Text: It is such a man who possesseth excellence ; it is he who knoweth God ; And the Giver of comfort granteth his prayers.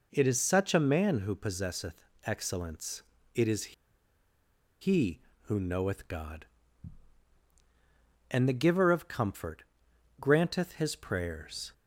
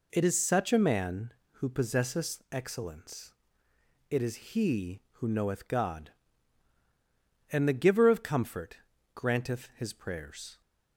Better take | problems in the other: second | pauses between "possesseth" and "excellence"; slight; at 1.9 s; 0.32 s long // pauses between "is" and "he"; at 3.7 s; 1.0 s long // pauses between "comfort" and "granteth"; noticeable; at 9.6 s; 0.56 s long; slight in the second

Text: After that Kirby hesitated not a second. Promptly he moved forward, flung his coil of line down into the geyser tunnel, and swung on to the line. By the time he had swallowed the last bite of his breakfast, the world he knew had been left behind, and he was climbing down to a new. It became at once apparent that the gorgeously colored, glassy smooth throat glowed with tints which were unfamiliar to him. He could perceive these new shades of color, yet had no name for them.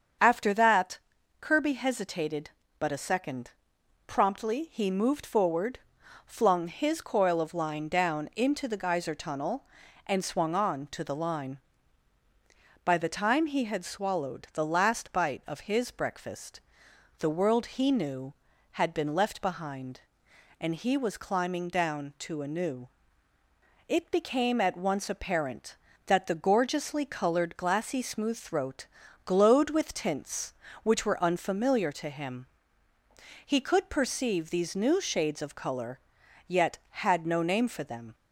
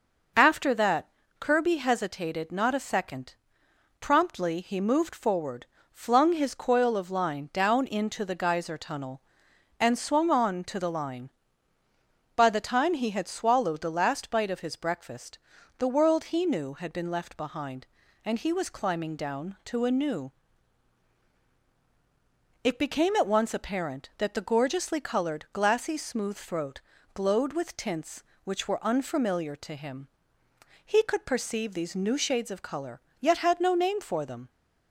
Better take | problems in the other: second | starts louder than the rest; strong; until 1.6 s; 7 dB // pauses between "that" and "Kirby"; at 0.9 s; 0.42 s long; slight in the second // says "but" for "not"; at 2.7 s // pauses between "throat" and "glowed"; at 28.8 s; 0.38 s long; slight in the second

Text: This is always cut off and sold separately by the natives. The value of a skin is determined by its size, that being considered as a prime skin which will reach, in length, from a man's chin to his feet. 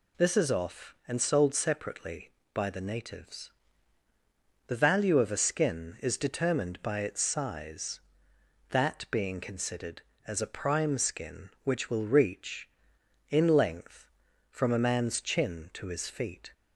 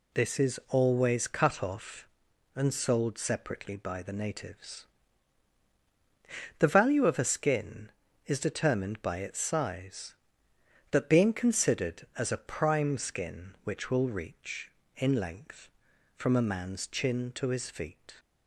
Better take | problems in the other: second | skips "always cut"; at 0.4 s

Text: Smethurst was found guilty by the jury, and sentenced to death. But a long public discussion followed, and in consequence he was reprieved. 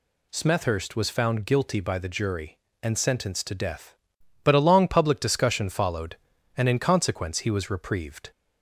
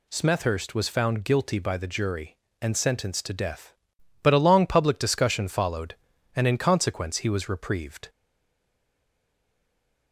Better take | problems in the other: first | stays silent after the last word; noticeable; from 8.0 s on; 2.1 s long

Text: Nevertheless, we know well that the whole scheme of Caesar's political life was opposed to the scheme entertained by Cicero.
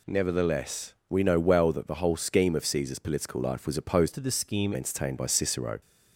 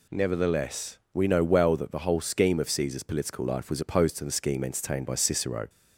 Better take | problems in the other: second | changes voice from "to" to "scheme"; from 4.1 to 4.7 s; 0.6 s long

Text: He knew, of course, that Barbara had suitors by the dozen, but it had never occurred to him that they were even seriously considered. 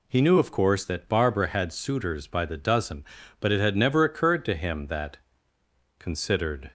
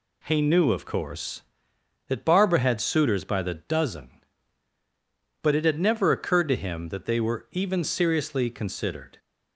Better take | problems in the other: second | skips "they were even seriously"; at 5.5 s

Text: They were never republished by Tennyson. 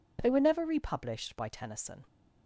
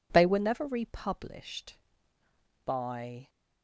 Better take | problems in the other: first | stops before "Tennyson"; at 3.2 s

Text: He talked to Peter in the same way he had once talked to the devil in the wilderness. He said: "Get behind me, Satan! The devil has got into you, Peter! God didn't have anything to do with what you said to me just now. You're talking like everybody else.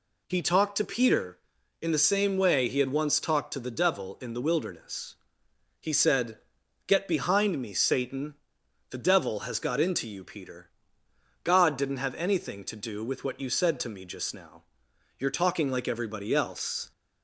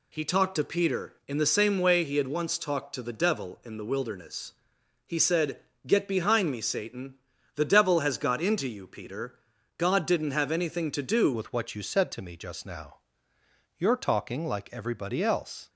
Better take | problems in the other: first | changes voice at "with"; from 11.3 s on; 4.3 s long

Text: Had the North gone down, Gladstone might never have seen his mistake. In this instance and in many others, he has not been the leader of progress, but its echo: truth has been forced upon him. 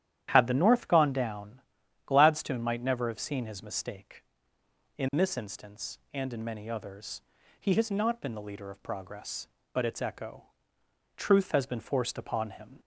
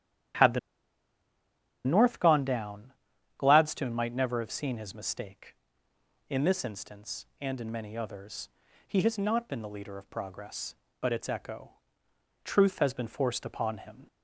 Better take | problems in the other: first | starts louder than the rest; strong; until 2.6 s; 11 dB; strong in the first // pauses between "the" and "North"; strong; at 0.5 s; 1.2 s long

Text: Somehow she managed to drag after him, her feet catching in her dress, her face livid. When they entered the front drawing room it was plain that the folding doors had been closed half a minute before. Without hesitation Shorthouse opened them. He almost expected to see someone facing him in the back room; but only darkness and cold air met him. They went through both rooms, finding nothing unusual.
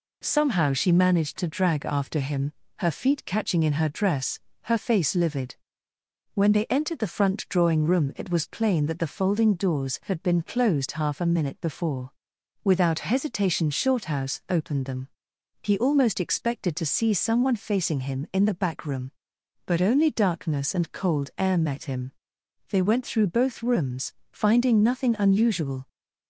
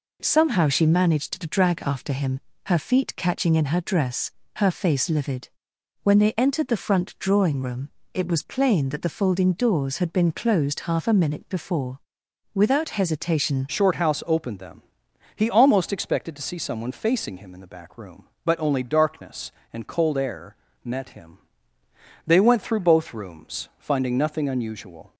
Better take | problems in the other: first | pauses between "room" and "it"; slight; at 7.8 s; 0.24 s long // changes voice at "Shorthouse"; from 13.6 s on; 11.5 s long // pauses between "air" and "met"; slight; at 20.5 s; 0.30 s long

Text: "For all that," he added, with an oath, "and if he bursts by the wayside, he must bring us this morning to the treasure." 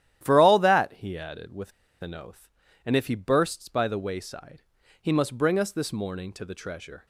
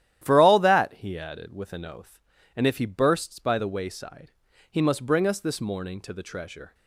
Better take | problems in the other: second | starts louder than the rest; strong; until 1.2 s; 12 dB; strong in the second // pauses between "with" and "an"; slight; at 1.7 s; 0.30 s long

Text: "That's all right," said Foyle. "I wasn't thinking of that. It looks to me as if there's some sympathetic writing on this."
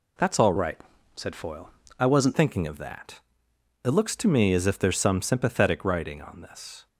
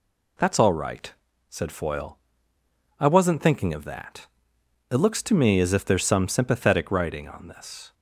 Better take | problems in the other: second | changes voice from "right" to "wasn't"; from 0.5 to 2.3 s; 1.8 s long

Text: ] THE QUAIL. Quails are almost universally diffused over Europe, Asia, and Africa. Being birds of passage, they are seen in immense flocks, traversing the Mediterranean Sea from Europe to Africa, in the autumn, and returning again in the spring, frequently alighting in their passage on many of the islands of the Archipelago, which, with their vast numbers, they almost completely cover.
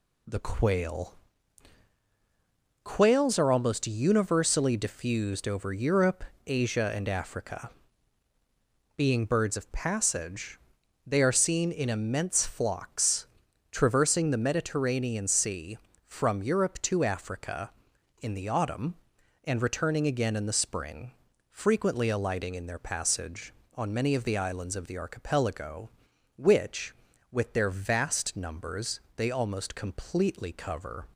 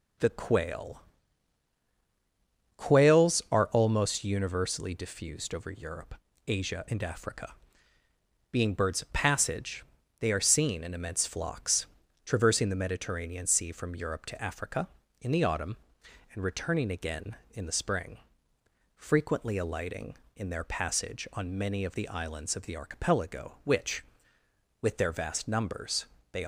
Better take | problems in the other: first | stops before "almost completely cover"; at 26.4 s

